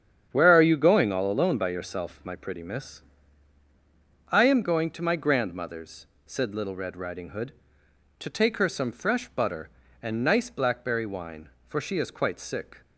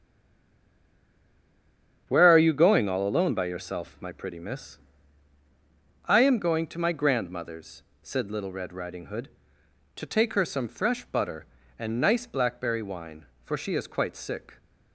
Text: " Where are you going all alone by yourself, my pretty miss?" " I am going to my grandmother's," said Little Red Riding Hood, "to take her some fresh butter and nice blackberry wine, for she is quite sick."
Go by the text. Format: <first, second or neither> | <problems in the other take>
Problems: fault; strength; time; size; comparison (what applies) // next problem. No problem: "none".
first | stays silent before the first word; noticeable; until 2.0 s; 2.0 s long // starts louder than the rest; strong; until 3.0 s; 8 dB; strong in the first